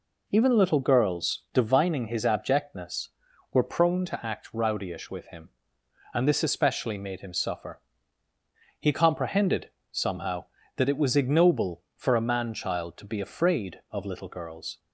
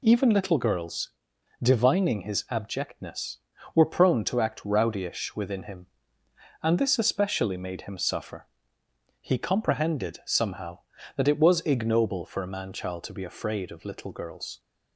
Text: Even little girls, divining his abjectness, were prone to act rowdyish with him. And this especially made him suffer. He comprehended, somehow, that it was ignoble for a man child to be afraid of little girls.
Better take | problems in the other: first | says "within" for "with"; at 5.3 s

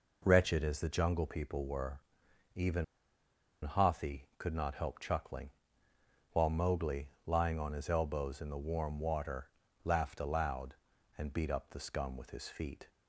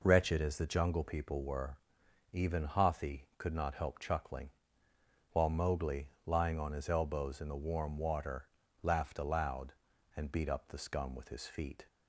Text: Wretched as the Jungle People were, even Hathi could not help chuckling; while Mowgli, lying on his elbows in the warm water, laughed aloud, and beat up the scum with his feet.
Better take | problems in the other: second | pauses between "even" and "Hathi"; noticeable; at 2.8 s; 0.80 s long

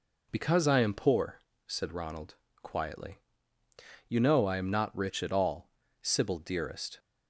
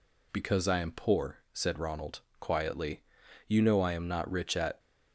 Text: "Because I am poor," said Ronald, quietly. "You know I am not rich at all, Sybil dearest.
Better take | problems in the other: first | stops before "all Sybil dearest"; at 4.7 s

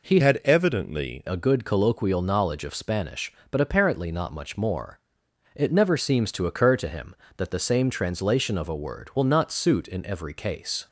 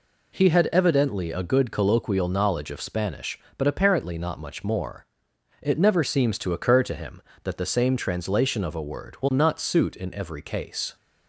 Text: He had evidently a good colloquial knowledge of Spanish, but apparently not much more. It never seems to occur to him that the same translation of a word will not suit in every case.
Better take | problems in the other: second | changes voice from "had" to "evidently"; from 0.1 to 1.2 s; 1.1 s long

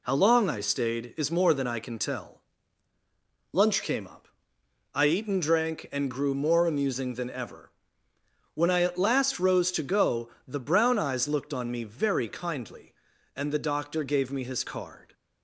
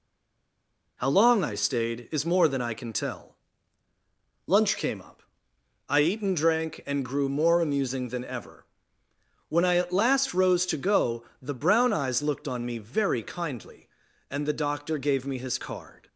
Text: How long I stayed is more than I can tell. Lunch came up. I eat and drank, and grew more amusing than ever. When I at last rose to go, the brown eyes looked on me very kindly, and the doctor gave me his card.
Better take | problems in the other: first | stays silent before the first word; until 0.9 s; 0.9 s long

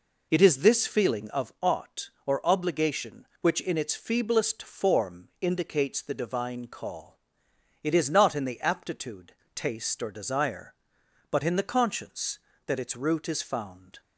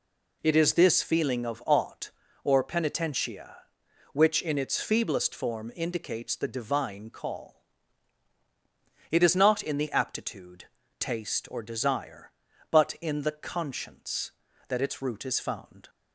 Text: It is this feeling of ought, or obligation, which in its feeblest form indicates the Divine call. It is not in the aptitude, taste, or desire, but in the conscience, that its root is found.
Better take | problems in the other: first | says "penitentia" for "obligation"; at 2.6 s

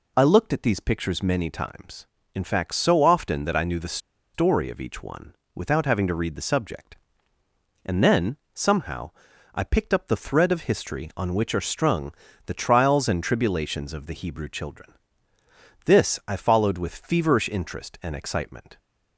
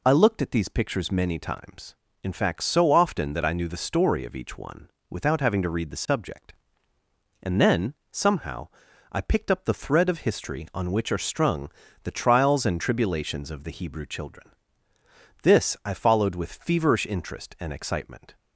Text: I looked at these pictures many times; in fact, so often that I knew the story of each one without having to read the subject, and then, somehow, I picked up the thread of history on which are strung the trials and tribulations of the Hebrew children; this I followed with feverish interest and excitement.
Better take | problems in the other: second | pauses between "the" and "story"; at 3.9 s; 0.36 s long // pauses between "one" and "without"; slight; at 5.3 s; 0.20 s long; slight in the second // pauses between "strung" and "the"; slight; at 12.1 s; 0.32 s long; slight in the second

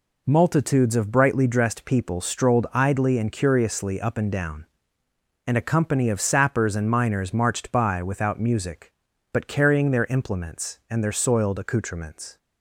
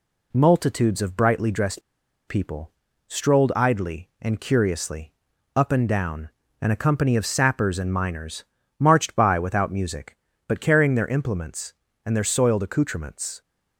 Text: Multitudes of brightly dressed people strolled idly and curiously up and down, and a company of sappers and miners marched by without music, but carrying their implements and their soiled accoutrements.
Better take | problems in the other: first | pauses between "dressed" and "people"; noticeable; at 1.8 s; 0.47 s long // pauses between "people" and "strolled"; at 2.7 s; 0.38 s long // pauses between "curiously" and "up"; at 5.1 s; 0.44 s long // pauses between "miners" and "marched"; slight; at 8.4 s; 0.34 s long

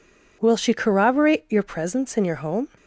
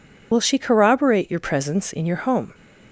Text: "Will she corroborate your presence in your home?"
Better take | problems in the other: first | loses the start of "Will"; at 0.3 s; 35 ms

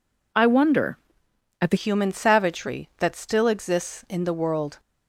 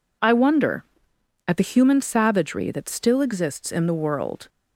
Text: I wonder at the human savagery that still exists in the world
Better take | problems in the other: second | changes voice at "human"; from 1.7 s on; 3.0 s long

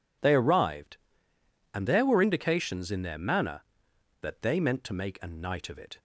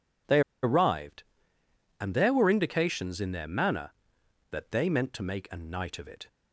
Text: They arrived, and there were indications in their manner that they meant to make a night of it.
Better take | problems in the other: first | pauses between "They" and "arrived"; slight; at 0.4 s; 0.22 s long

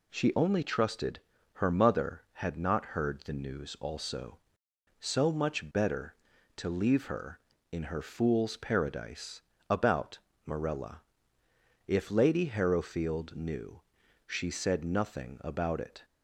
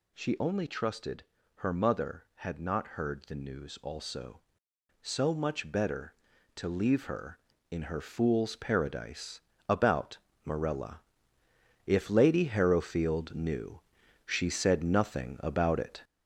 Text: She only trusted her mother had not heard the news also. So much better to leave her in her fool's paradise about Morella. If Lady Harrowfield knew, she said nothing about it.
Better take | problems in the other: first | gets louder; noticeable; throughout; 5.5 dB // pauses between "trusted" and "her"; slight; at 1.2 s; 0.32 s long; slight in the first // pauses between "paradise" and "about"; slight; at 9.3 s; 0.30 s long; slight in the first // pauses between "about" and "Morella"; slight; at 10.1 s; 0.26 s long; slight in the first

